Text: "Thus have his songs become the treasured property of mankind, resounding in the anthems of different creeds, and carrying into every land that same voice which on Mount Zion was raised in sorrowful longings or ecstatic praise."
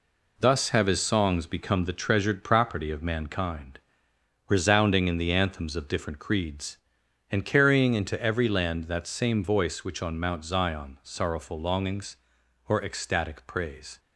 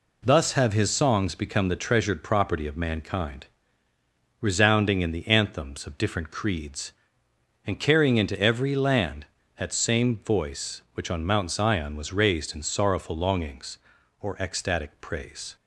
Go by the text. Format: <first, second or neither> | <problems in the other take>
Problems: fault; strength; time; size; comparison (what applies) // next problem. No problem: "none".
second | skips "was raised in"; at 11.0 s